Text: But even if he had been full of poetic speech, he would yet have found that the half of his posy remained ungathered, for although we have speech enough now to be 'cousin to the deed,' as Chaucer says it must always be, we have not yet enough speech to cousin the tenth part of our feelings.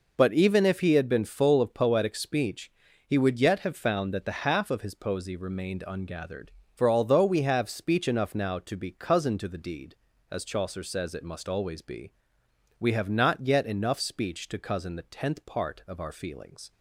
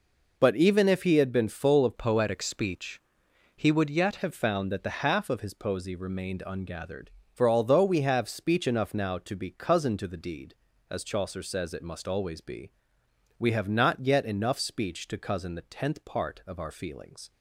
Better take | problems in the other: first | changes voice from "poetic" to "yet"; from 1.9 to 4.1 s; 2.2 s long

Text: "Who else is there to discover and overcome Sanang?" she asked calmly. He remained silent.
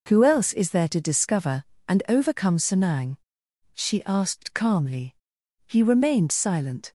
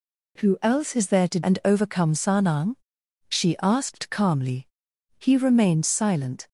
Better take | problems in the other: first | skips "discover"; at 1.4 s

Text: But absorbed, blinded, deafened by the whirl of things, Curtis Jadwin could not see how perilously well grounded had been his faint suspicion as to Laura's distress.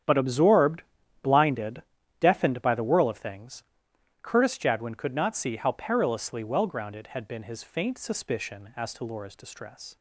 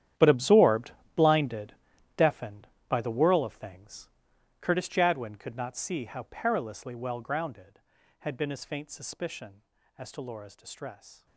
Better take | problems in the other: first | gets quieter; strong; throughout; 16.5 dB // starts louder than the rest; strong; until 1.4 s; 10.5 dB; strong in the first

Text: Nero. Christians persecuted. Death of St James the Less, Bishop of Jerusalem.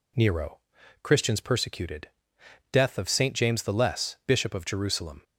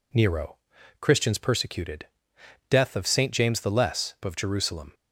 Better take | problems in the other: first | skips "Bishop"; at 4.1 s

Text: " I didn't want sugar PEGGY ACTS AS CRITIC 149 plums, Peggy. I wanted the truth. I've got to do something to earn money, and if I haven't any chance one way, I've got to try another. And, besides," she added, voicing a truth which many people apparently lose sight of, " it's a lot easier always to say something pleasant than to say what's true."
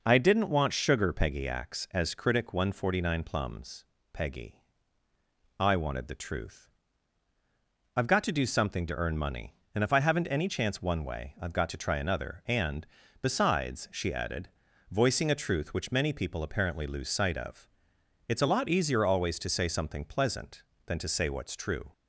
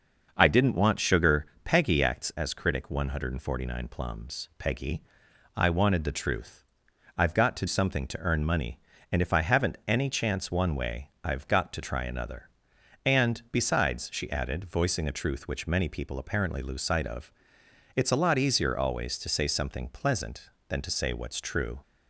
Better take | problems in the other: first | pauses between "sugar" and "PEGGY"; slight; at 1.4 s; 0.16 s long // skips "do"; at 7.6 s

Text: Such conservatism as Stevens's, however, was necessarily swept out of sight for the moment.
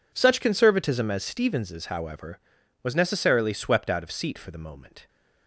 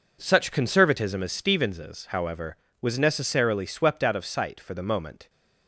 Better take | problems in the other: second | says "seat" for "sight"; at 4.1 s

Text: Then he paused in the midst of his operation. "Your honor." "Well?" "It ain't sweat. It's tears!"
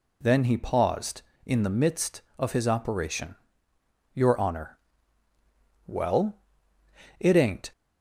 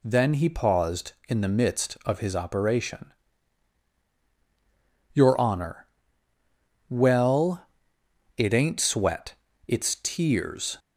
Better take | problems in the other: second | stops before "sweat It's tears"; at 7.7 s

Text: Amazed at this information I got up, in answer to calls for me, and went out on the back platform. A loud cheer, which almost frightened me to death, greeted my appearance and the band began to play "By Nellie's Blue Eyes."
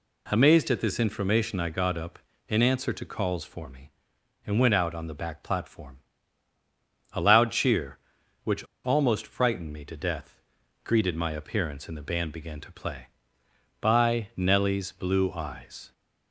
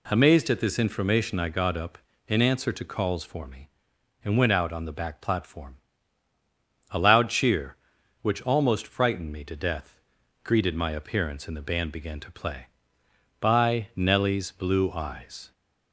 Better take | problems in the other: second | pauses between "which" and "almost"; slight; at 8.6 s; 0.19 s long

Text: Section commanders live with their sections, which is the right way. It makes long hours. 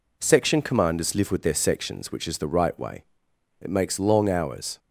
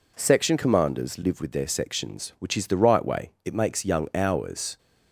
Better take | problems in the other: first | says "young" for "long"; at 3.8 s

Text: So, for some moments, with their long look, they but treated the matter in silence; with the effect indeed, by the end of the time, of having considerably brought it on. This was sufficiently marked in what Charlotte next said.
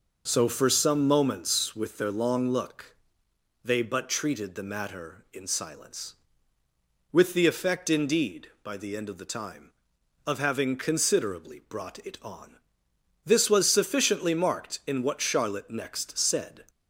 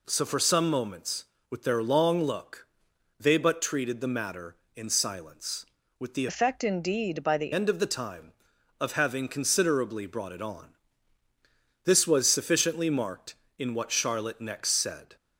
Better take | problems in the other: first | changes voice from "effect" to "the"; from 6.2 to 7.5 s; 1.3 s long

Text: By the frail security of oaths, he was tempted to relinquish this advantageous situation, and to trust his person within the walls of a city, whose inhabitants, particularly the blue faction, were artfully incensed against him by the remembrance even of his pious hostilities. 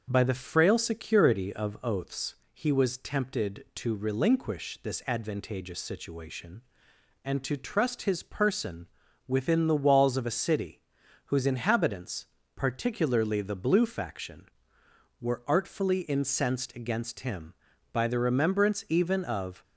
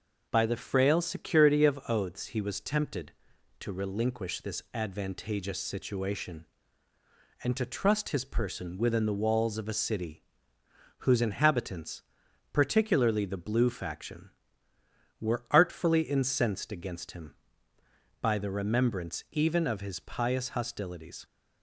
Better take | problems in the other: second | starts louder than the rest; until 1.1 s; 6 dB // pauses between "person" and "within"; at 8.8 s; 0.40 s long // stops before "his pious hostilities"; at 19.6 s

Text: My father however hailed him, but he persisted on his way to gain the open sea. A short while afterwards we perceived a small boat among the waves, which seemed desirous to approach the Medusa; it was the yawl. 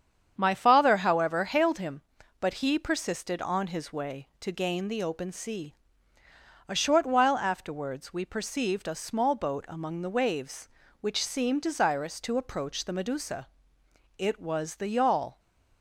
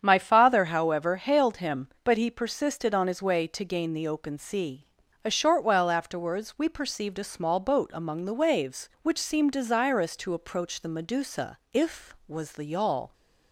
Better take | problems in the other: first | starts louder than the rest; strong; until 1.0 s; 8 dB; strong in the first // says "if" for "it"; at 11.7 s

